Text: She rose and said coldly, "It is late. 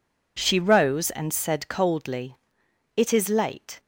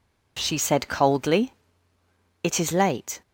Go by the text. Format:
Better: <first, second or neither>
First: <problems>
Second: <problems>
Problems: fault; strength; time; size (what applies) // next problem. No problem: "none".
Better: first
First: none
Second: skips "rose and"; at 0.5 s